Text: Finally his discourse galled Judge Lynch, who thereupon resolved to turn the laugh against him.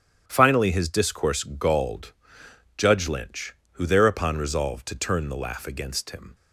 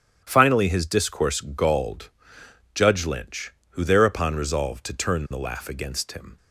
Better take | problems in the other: neither | starts louder than the rest; strong; the same in both // pauses between "galled" and "Judge"; noticeable; the same in both

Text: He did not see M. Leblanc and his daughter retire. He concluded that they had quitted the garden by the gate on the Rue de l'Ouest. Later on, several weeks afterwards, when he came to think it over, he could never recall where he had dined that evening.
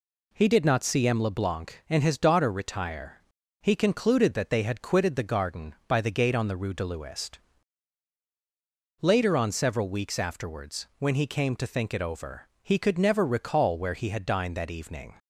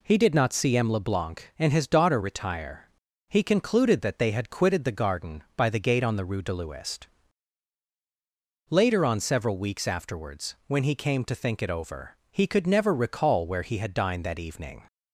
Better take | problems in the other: neither | none

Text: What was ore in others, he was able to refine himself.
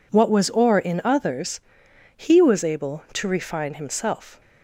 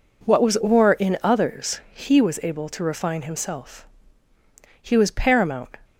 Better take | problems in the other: first | goes on to say "He was paramount"; noticeable; from 4.7 s on; 0.98 s long

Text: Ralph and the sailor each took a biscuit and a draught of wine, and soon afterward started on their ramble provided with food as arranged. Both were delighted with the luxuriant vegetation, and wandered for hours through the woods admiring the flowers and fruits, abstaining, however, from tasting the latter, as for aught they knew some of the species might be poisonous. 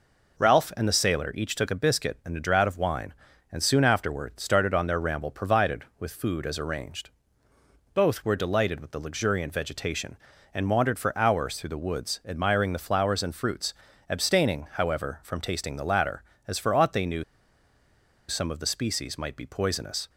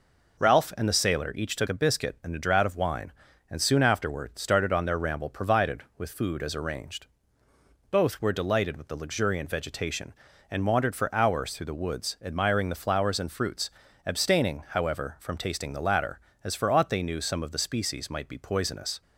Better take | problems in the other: second | pauses between "knew" and "some"; at 17.2 s; 1.0 s long

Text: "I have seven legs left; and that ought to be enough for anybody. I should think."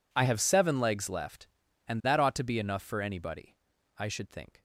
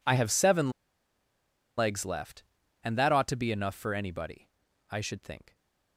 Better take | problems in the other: first | pauses between "seven" and "legs"; at 0.6 s; 1.0 s long

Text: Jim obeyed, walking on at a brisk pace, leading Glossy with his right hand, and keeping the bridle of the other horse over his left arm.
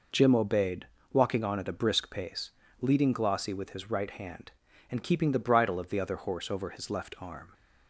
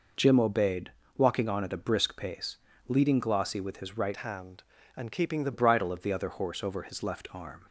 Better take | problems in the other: first | changes voice from "hand" to "the"; from 4.1 to 5.5 s; 1.4 s long

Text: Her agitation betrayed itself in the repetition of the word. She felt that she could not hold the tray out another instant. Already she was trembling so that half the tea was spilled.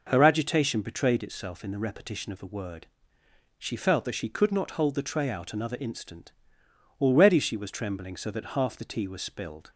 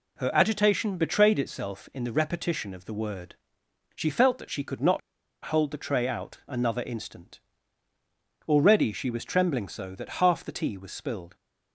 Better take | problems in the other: first | pauses between "not" and "hold"; at 5.0 s; 0.44 s long

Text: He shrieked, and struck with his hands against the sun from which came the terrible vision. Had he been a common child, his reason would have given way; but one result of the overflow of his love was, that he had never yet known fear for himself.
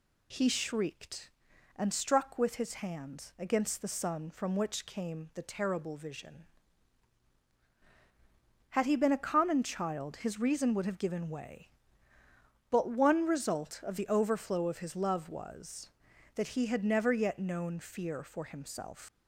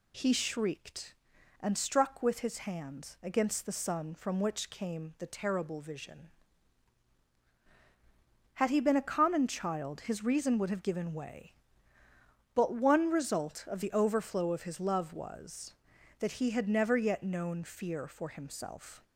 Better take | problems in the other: second | leaves "himself" unfinished; at 19.0 s; 105 ms

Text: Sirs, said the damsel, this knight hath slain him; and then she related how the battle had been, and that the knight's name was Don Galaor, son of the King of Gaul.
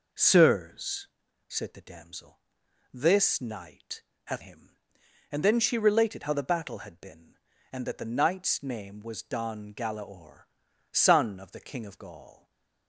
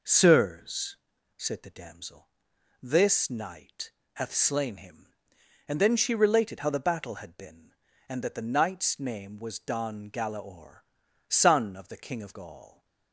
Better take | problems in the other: second | pauses between "knight" and "hath"; slight; at 4.0 s; 0.22 s long; slight in the second // skips "slain"; at 4.4 s // stays silent after the last word; slight; from 12.3 s on; 0.5 s long

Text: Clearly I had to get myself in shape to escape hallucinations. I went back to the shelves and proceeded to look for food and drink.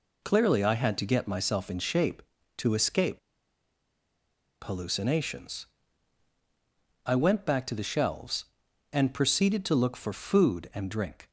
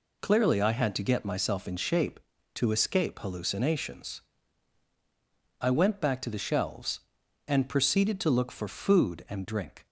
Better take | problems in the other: second | pauses between "escape" and "hallucinations"; strong; at 3.1 s; 1.4 s long

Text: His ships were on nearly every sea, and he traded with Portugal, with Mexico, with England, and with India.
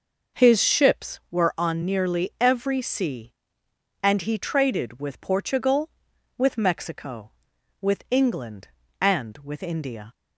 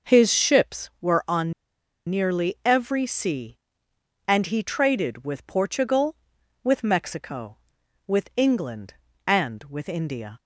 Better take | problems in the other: first | pauses between "on" and "nearly"; noticeable; at 1.5 s; 0.56 s long

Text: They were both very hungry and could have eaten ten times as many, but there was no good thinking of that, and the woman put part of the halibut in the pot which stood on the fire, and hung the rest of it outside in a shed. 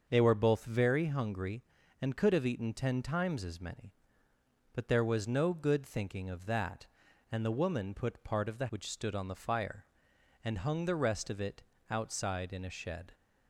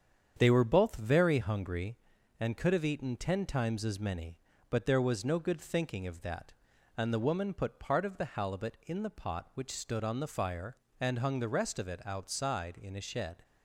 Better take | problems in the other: second | starts louder than the rest; until 1.0 s; 6.5 dB; strong in the second // skips "halibut in the pot"; at 8.6 s // pauses between "it" and "outside"; slight; at 11.6 s; 0.28 s long

